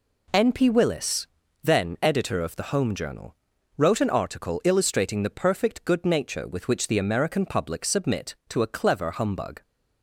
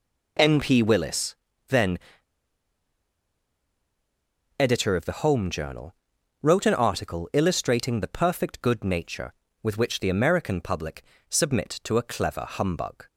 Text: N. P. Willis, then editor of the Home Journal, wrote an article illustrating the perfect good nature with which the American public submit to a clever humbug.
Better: first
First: none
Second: pauses between "then" and "editor"; strong; at 1.9 s; 2.5 s long // pauses between "public" and "submit"; slight; at 11.0 s; 0.24 s long

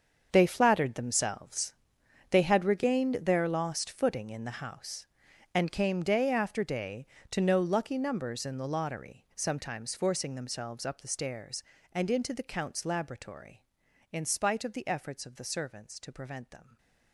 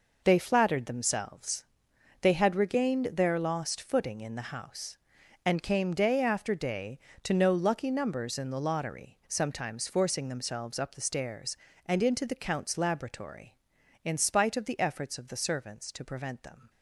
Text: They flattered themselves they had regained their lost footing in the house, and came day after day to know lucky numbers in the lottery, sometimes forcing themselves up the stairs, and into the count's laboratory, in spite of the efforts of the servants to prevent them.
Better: second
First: gets quieter; strong; throughout; 14 dB // pauses between "themselves" and "they"; noticeable; at 1.7 s; 0.58 s long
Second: pauses between "themselves" and "they"; noticeable; at 1.6 s; 0.58 s long

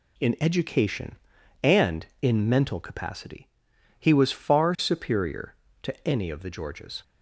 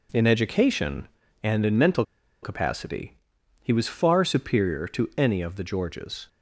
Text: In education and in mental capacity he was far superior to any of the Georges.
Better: first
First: pauses between "capacity" and "he"; noticeable; at 3.4 s; 0.52 s long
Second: pauses between "mental" and "capacity"; at 2.0 s; 0.40 s long // pauses between "capacity" and "he"; noticeable; at 3.1 s; 0.46 s long

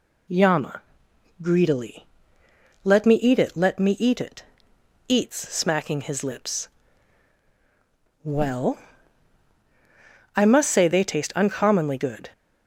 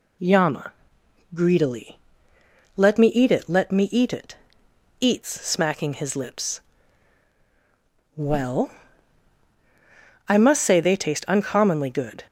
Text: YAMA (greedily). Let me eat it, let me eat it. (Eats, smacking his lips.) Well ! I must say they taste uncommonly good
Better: neither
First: none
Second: none

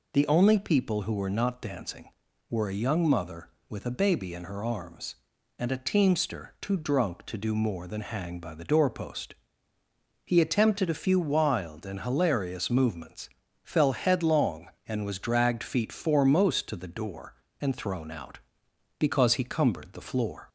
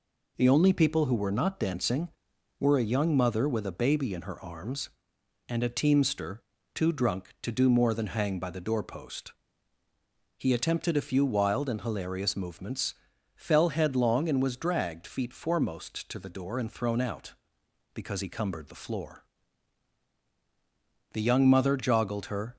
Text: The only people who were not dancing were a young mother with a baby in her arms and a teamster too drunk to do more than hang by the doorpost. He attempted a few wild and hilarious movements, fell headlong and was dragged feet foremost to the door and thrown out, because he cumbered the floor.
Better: first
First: none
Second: pauses between "teamster" and "too"; slight; at 6.4 s; 0.32 s long // goes on to say "The young mother joggled her"; from 21.1 s on; 1.4 s long

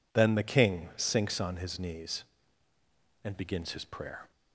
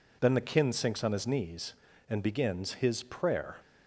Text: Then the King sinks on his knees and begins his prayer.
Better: first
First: none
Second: says "Kin" for "King"; at 0.4 s

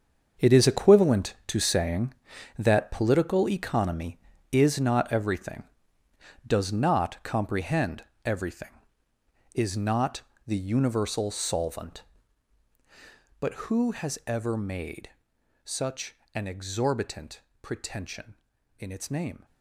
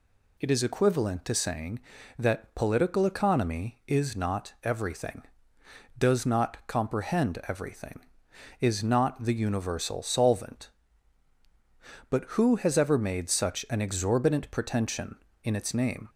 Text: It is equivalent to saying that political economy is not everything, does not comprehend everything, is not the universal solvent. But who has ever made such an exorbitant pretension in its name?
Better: second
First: gets quieter; strong; throughout; 12.5 dB // pauses between "comprehend" and "everything"; slight; at 8.0 s; 0.22 s long // pauses between "not" and "the"; slight; at 10.2 s; 0.24 s long // pauses between "made" and "such"; noticeable; at 15.1 s; 0.52 s long // pauses between "such" and "an"; slight; at 16.1 s; 0.18 s long // pauses between "exorbitant" and "pretension"; slight; at 17.4 s; 0.20 s long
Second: none

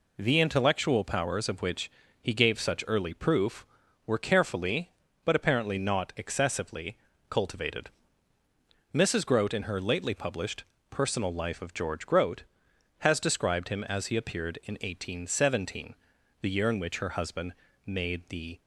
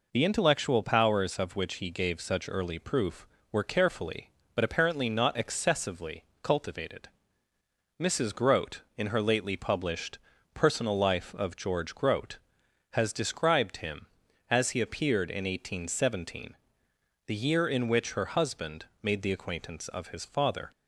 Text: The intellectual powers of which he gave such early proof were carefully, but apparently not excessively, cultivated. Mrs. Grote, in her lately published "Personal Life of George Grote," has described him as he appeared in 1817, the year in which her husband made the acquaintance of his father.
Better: second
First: pauses between "which" and "he"; slight; at 1.8 s; 0.32 s long // pauses between "published" and "Personal"; slight; at 10.6 s; 0.26 s long // pauses between "husband" and "made"; slight; at 17.5 s; 0.32 s long // stops before "acquaintance of his father"; at 18.6 s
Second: pauses between "published" and "Personal"; slight; at 10.1 s; 0.36 s long // pauses between "husband" and "made"; slight; at 18.8 s; 0.16 s long

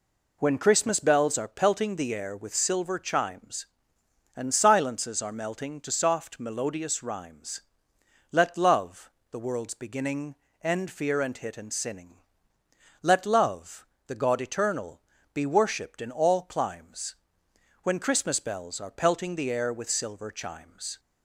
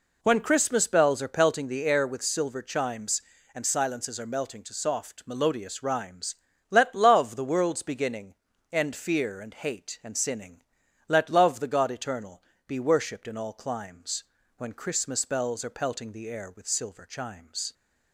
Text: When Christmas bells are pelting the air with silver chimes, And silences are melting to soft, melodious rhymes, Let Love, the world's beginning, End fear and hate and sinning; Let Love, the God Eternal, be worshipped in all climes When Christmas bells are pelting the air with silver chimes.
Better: second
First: says "hit" for "hate"; at 11.3 s // pauses between "climes" and "When"; noticeable; at 17.1 s; 0.68 s long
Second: pauses between "climes" and "When"; slight; at 14.2 s; 0.34 s long

